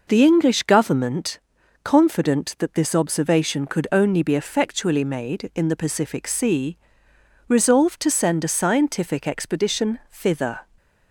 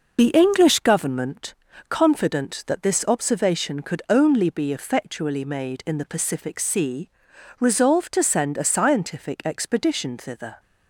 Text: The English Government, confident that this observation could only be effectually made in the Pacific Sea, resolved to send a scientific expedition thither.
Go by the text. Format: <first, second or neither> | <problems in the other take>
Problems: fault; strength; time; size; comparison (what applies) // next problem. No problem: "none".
first | loses the start of "The"; at 0.1 s; 45 ms